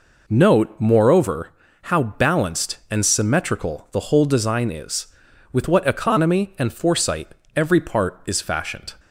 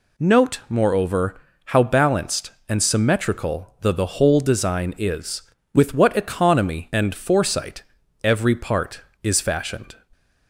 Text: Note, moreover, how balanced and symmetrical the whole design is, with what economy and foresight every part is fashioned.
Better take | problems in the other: first | says "the" twice; at 3.9 s // pauses between "foresight" and "every"; at 7.8 s; 0.40 s long; slight in the first

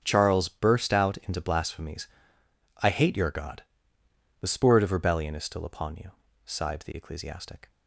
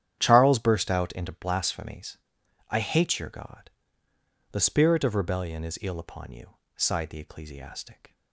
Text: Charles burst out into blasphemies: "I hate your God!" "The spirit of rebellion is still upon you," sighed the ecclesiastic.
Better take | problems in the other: first | starts louder than the rest; strong; until 1.2 s; 10 dB; also in the first // says "ill" for "still"; at 5.8 s

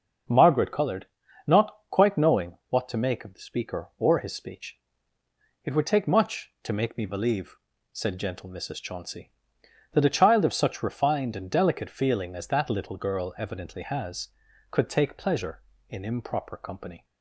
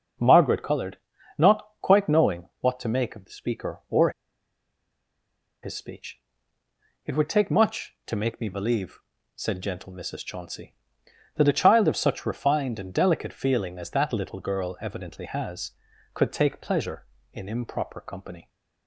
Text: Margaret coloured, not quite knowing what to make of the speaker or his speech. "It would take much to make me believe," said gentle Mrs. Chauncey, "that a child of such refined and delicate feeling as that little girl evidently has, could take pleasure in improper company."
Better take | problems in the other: first | starts louder than the rest; until 1.6 s; 6 dB; also in the first // pauses between "not" and "quite"; slight; at 1.6 s; 0.16 s long; slight in the first // pauses between "or" and "his"; strong; at 4.0 s; 1.5 s long

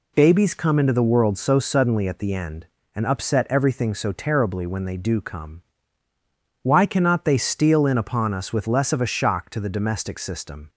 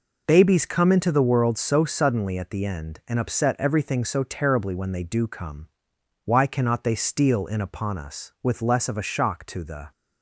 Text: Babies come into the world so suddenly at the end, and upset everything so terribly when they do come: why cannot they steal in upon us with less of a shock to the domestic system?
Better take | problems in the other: first | stops before "domestic system"; at 9.9 s

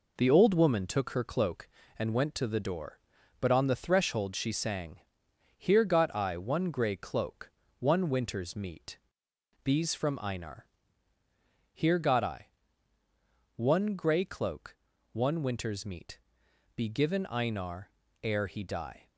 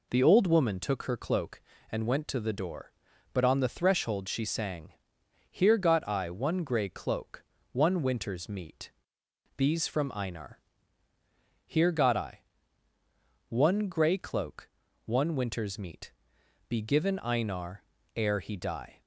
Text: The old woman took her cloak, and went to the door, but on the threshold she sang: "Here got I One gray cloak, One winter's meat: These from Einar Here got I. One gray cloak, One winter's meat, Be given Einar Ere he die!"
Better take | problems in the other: second | gets quieter; noticeable; throughout; 5.5 dB // pauses between "Einar" and "Here"; at 10.6 s; 1.0 s long; also in the second // pauses between "Einar" and "Ere"; slight; at 17.8 s; 0.32 s long; slight in the second

